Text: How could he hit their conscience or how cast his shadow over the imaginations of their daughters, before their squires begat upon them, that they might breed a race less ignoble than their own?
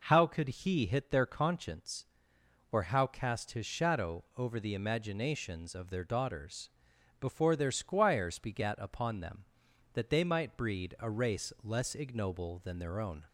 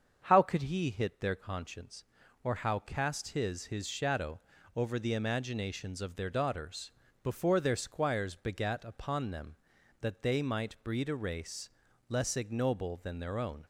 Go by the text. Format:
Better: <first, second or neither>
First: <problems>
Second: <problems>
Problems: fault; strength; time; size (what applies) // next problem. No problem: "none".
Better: first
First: none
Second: starts louder than the rest; until 1.2 s; 7 dB // says "his" twice; at 3.6 s // pauses between "shadow" and "over"; slight; at 4.3 s; 0.34 s long // pauses between "race" and "less"; at 11.6 s; 0.38 s long